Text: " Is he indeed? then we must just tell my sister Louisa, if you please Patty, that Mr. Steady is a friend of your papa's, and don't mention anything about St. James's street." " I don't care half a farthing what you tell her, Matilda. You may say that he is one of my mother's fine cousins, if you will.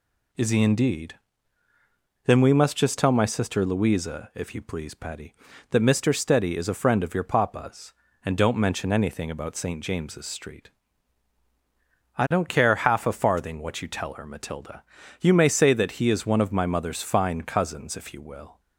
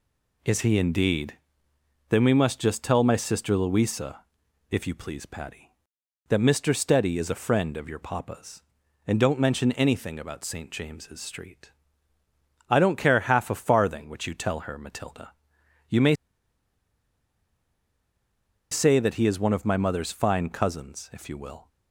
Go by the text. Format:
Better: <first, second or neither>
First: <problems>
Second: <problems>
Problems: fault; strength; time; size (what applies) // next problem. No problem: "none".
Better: first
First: none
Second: pauses between "may" and "say"; strong; at 16.1 s; 2.5 s long